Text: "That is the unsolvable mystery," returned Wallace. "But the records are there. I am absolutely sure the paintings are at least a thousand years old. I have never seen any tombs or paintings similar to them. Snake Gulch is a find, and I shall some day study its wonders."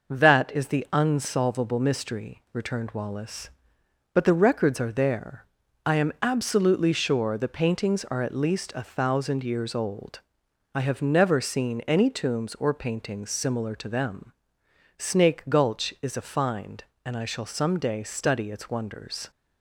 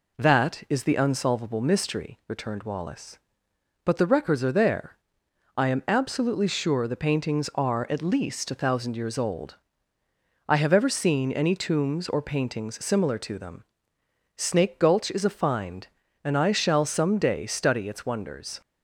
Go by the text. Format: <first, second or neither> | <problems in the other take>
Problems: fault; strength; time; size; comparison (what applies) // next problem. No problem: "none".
first | says "ever" for "never"; at 10.7 s